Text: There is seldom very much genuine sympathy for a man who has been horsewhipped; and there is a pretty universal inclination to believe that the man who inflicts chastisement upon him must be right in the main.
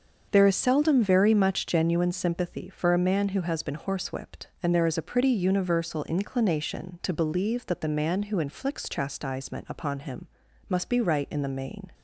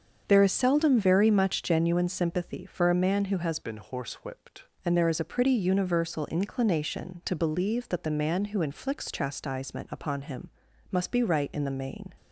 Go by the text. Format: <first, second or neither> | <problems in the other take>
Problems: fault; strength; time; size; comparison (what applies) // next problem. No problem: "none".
first | starts louder than the rest; until 1.2 s; 7 dB; also in the first // changes voice from "been" to "horsewhipped"; from 3.6 to 4.6 s; 1.0 s long // pauses between "him" and "must"; at 10.4 s; 0.40 s long; also in the first